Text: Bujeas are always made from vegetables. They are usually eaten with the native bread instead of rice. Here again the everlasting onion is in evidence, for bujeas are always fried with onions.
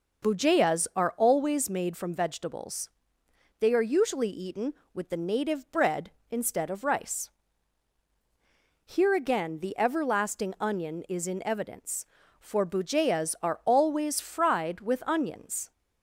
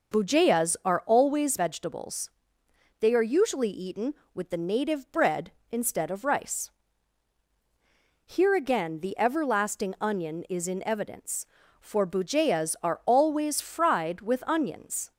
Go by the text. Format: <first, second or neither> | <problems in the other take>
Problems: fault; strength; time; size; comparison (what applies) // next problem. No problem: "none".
first | skips "made from"; at 1.5 s